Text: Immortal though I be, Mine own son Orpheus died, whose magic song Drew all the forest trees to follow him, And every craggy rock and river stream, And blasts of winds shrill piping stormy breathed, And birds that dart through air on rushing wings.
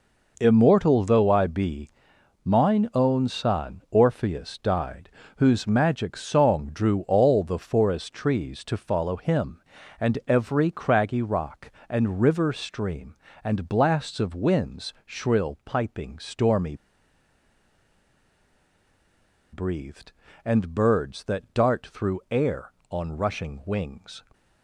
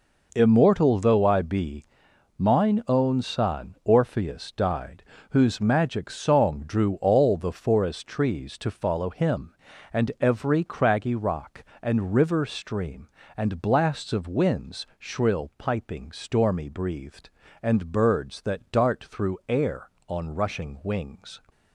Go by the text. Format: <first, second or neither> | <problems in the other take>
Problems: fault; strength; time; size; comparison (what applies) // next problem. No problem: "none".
second | pauses between "stormy" and "breathed"; strong; at 16.7 s; 2.7 s long